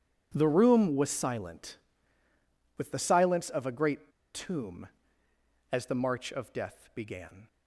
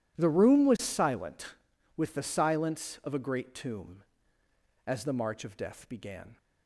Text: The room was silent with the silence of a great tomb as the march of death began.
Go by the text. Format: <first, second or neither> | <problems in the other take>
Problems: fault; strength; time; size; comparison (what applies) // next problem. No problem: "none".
second | pauses between "great" and "tomb"; slight; at 4.1 s; 0.23 s long